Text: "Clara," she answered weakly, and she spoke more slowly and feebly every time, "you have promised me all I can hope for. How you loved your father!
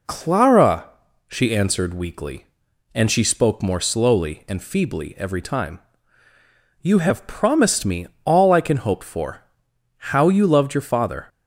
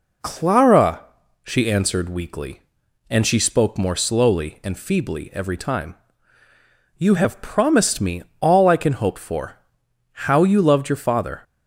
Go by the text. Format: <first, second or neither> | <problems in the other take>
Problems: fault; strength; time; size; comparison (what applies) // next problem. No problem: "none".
neither | pauses between "me" and "all"; slight; the same in both